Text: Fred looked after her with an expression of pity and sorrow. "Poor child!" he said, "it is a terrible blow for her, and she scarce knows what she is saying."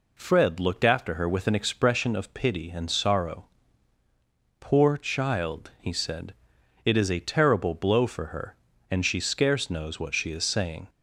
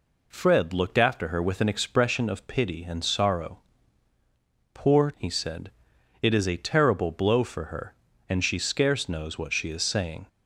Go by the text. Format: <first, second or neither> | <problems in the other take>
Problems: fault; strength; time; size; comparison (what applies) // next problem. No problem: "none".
first | skips "child"; at 5.1 s